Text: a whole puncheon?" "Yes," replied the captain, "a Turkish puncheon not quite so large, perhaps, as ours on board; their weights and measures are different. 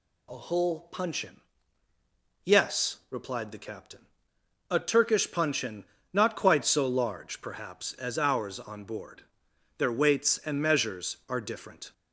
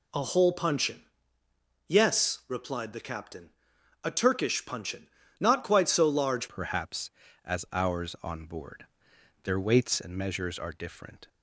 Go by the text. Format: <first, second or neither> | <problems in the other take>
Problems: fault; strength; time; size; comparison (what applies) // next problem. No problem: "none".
first | pauses between "puncheon" and "not"; slight; at 5.0 s; 0.30 s long; slight in the first // changes voice at "perhaps"; from 6.4 s on; 4.8 s long